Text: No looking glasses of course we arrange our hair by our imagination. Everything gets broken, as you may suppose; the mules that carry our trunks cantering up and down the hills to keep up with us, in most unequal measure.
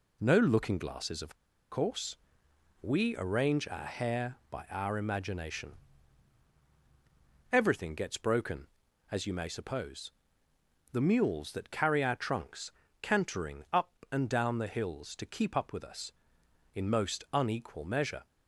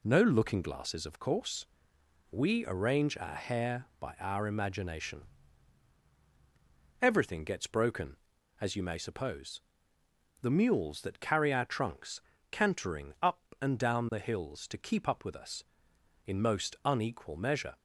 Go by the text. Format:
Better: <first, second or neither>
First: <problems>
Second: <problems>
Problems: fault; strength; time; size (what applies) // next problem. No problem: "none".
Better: second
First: pauses between "of" and "course"; slight; at 1.3 s; 0.34 s long // pauses between "course" and "we"; noticeable; at 2.1 s; 0.68 s long // pauses between "trunks" and "cantering"; slight; at 12.7 s; 0.30 s long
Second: pauses between "course" and "we"; noticeable; at 1.6 s; 0.68 s long // pauses between "trunks" and "cantering"; slight; at 12.1 s; 0.30 s long